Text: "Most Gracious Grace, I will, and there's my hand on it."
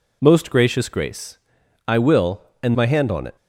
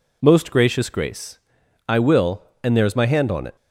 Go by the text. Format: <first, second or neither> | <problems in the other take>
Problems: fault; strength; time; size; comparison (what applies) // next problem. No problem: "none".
second | skips "there's"; at 2.7 s